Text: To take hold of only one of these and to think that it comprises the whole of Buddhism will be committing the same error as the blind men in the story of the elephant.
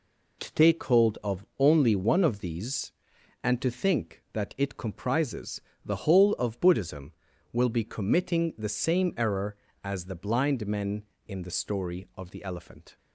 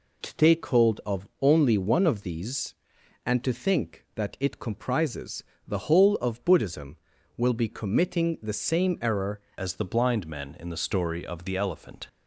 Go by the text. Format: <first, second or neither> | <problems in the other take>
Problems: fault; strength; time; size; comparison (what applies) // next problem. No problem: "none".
first | pauses between "comprises" and "the"; slight; at 5.4 s; 0.24 s long; slight in the first // changes voice at "as"; from 9.5 s on; 2.5 s long